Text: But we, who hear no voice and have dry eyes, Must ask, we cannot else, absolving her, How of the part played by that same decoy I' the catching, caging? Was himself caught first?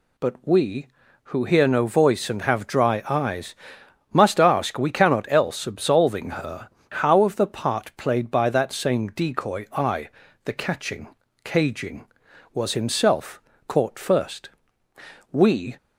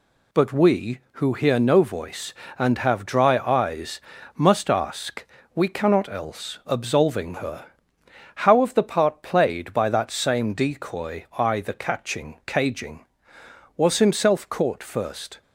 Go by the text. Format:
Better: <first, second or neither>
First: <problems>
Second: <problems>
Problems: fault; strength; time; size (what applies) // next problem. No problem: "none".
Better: second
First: pauses between "I" and "the"; slight; at 10.0 s; 0.36 s long // pauses between "himself" and "caught"; slight; at 13.3 s; 0.28 s long // goes on to say "We"; slight; from 15.3 s on; 0.46 s long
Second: none